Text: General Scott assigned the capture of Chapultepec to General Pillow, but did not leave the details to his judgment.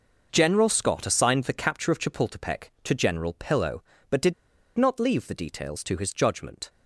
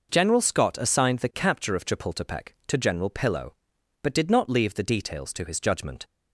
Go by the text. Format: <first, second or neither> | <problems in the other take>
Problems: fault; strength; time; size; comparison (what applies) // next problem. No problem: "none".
second | pauses between "did" and "not"; at 4.3 s; 0.43 s long